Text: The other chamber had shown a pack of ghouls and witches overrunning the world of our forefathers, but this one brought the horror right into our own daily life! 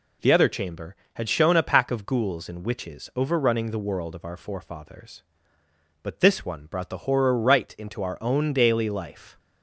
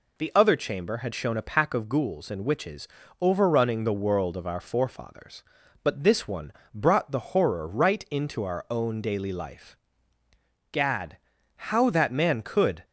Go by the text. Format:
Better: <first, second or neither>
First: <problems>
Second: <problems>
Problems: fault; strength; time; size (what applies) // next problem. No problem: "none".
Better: first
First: none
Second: pauses between "witches" and "overrunning"; slight; at 2.8 s; 0.34 s long // pauses between "one" and "brought"; slight; at 6.5 s; 0.20 s long // goes on to say "Gad how that man could"; strong; from 10.7 s on; 2.1 s long